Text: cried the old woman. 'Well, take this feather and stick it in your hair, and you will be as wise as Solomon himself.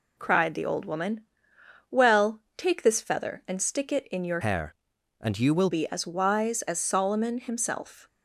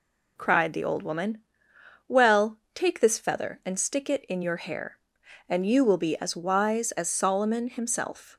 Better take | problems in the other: second | changes voice from "hair" to "will"; from 4.4 to 5.6 s; 1.2 s long

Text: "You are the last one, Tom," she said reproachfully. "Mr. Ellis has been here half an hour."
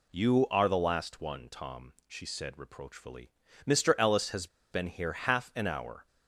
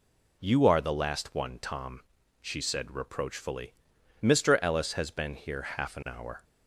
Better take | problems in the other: second | pauses between "has" and "been"; slight; at 4.4 s; 0.25 s long

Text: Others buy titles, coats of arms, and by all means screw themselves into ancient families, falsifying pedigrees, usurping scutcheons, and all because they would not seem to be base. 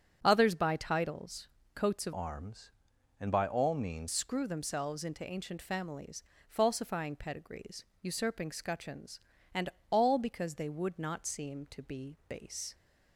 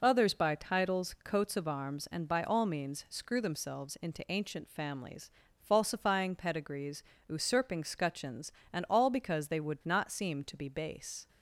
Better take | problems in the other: second | starts louder than the rest; strong; until 1.2 s; 8 dB // changes voice from "arms" to "means"; from 2.1 to 4.0 s; 1.9 s long // pauses between "and" and "all"; slight; at 9.7 s; 0.20 s long

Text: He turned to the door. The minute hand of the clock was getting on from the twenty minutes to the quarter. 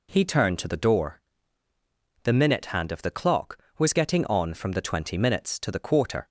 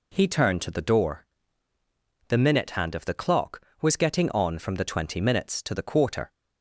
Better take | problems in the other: neither | none

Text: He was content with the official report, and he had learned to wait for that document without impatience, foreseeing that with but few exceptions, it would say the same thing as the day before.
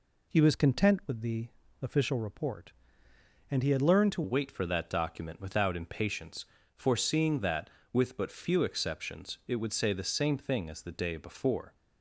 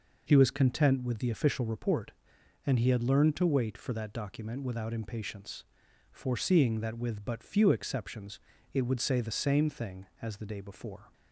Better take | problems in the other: second | pauses between "the" and "official"; slight; at 1.4 s; 0.34 s long // changes voice at "wait"; from 4.2 s on; 7.5 s long

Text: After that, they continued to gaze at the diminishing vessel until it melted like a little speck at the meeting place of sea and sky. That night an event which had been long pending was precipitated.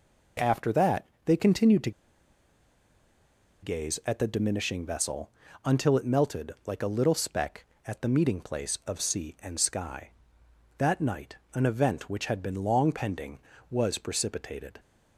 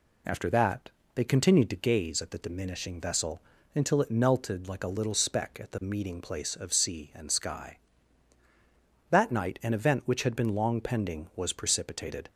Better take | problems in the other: second | pauses between "to" and "gaze"; strong; at 1.9 s; 1.7 s long // pauses between "vessel" and "until"; slight; at 5.2 s; 0.36 s long; slight in the second // pauses between "night" and "an"; slight; at 11.3 s; 0.18 s long

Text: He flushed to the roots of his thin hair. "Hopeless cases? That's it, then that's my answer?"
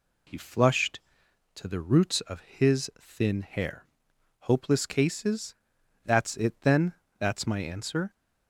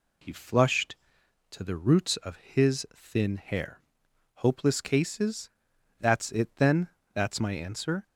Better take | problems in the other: neither | pauses between "then" and "that's"; slight; the same in both

